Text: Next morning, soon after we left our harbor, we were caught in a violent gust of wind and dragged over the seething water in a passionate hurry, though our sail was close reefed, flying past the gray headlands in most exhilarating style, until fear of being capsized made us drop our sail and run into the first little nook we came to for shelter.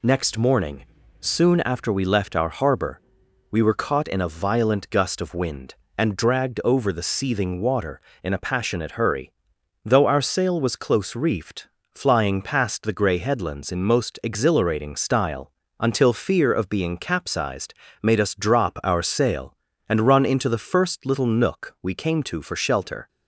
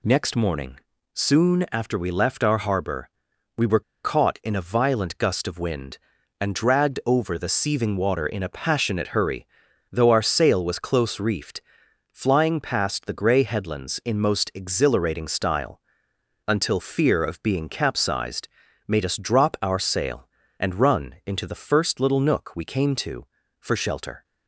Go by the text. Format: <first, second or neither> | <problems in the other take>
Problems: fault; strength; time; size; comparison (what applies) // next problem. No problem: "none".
first | pauses between "were" and "caught"; slight; at 3.8 s; 0.21 s long // pauses between "capsized" and "made"; at 18.4 s; 0.38 s long; slight in the first